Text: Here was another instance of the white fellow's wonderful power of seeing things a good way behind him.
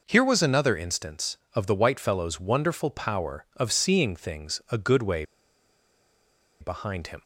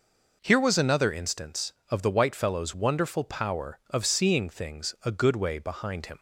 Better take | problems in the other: second | pauses between "way" and "behind"; strong; at 5.2 s; 1.3 s long

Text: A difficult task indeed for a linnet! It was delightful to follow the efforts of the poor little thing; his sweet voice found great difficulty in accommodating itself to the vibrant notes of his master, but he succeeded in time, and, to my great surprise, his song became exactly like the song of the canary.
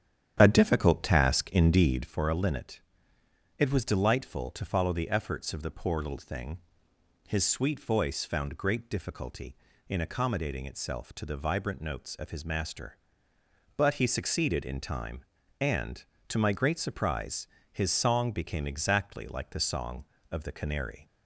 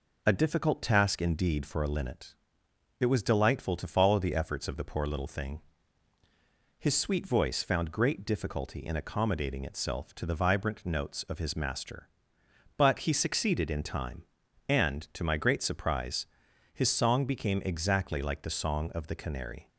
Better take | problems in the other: second | starts louder than the rest; strong; until 2.1 s; 9.5 dB

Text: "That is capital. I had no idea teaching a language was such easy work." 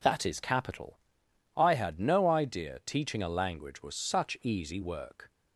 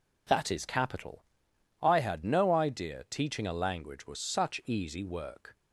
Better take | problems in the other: neither | none

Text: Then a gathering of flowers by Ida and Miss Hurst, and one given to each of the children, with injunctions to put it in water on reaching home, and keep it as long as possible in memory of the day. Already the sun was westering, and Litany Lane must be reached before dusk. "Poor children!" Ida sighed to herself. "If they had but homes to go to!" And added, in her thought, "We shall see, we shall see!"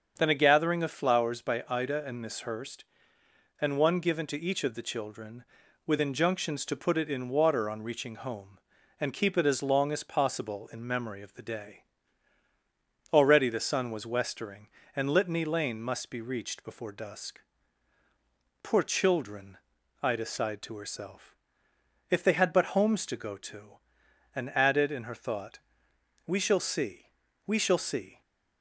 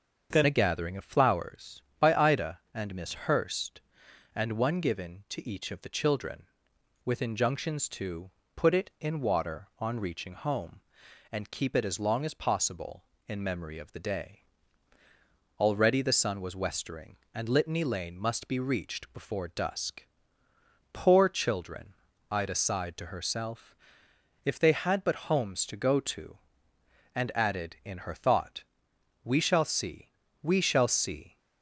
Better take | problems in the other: first | starts louder than the rest; until 1.3 s; 7 dB; also in the first // changes voice at "a"; from 0.4 s on; 30.9 s long // pauses between "to" and "put"; slight; at 8.2 s; 0.24 s long

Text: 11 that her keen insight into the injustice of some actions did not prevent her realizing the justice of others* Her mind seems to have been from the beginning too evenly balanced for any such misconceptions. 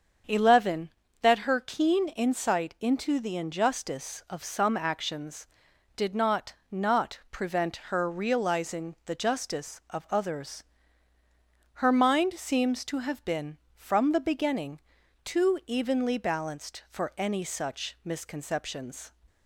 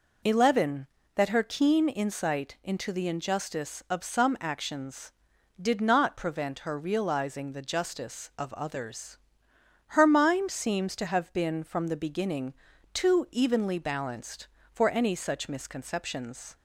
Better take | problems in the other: second | starts louder than the rest; until 1.5 s; 7 dB // says "not" twice; at 6.7 s // pauses between "others" and "Her"; at 10.6 s; 1.1 s long; noticeable in the second // pauses between "beginning" and "too"; noticeable; at 14.8 s; 0.46 s long; also in the second

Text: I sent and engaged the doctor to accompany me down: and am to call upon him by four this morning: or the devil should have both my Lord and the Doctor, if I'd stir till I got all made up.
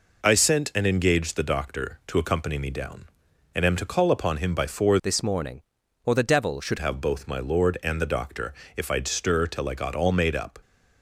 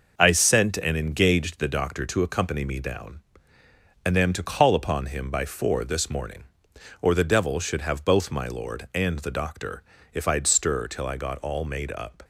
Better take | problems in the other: second | changes voice from "this" to "should"; from 5.0 to 6.7 s; 1.7 s long

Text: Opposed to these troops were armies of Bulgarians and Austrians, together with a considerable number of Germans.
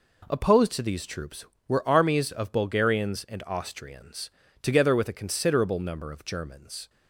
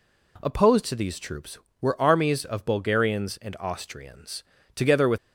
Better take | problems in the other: first | stops before "a considerable number of Germans"; at 5.1 s

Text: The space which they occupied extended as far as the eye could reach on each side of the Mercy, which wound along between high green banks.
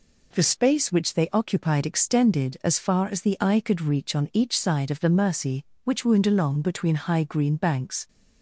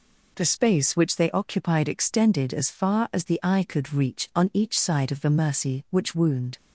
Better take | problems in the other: first | stops before "along between high green banks"; at 6.5 s

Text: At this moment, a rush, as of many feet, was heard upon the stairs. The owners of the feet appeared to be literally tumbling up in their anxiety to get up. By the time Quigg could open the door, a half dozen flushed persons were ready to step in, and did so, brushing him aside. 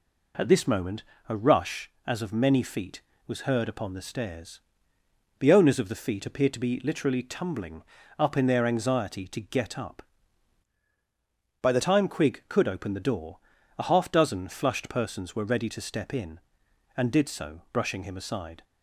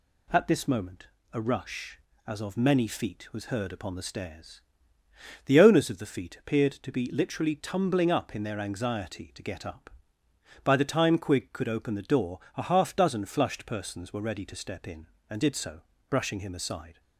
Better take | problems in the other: second | pauses between "tumbling" and "up"; slight; at 7.8 s; 0.36 s long // changes voice from "By" to "the"; from 11.5 to 11.8 s; 0.3 s long

